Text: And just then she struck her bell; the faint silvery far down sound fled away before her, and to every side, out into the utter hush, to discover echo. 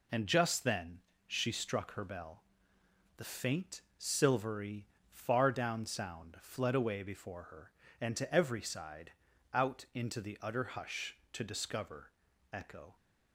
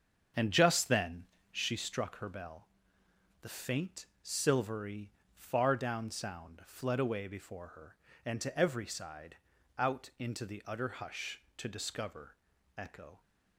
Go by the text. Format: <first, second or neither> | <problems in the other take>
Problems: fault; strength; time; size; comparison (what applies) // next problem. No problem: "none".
first | starts louder than the rest; strong; until 1.7 s; 7.5 dB // pauses between "then" and "she"; slight; at 1.2 s; 0.28 s long; slight in the first // pauses between "faint" and "silvery"; slight; at 4.0 s; 0.18 s long; slight in the first // pauses between "silvery" and "far"; slight; at 5.1 s; 0.24 s long; slight in the first // pauses between "discover" and "echo"; at 12.3 s; 0.42 s long; also in the first